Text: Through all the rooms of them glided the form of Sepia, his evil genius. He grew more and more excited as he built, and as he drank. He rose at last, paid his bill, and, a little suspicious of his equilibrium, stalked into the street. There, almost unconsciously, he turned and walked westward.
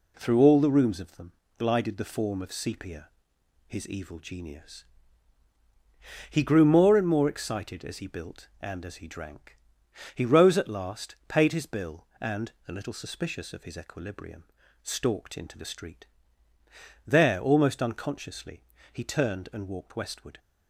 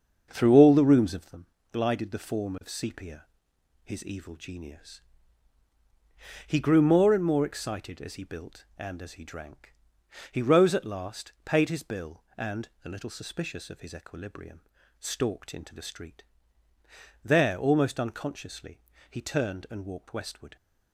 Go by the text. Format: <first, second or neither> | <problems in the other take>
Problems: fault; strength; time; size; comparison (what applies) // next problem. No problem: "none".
first | starts louder than the rest; until 1.3 s; 7 dB // pauses between "them" and "glided"; slight; at 1.4 s; 0.26 s long; slight in the first